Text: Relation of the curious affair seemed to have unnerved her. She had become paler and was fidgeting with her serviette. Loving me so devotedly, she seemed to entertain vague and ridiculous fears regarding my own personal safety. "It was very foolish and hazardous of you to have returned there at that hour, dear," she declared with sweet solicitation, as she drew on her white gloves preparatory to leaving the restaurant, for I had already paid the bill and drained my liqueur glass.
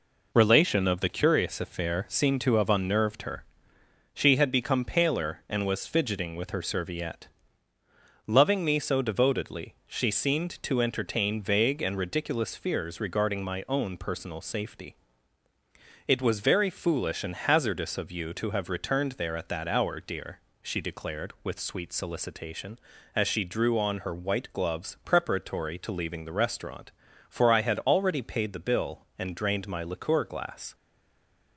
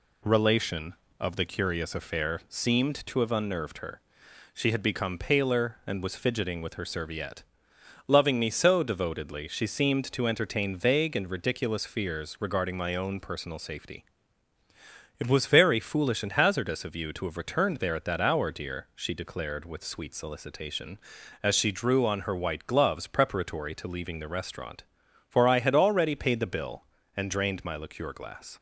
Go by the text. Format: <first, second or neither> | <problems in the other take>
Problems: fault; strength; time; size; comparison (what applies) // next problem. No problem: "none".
second | stays silent after the last word; slight; from 30.7 s on; 0.8 s long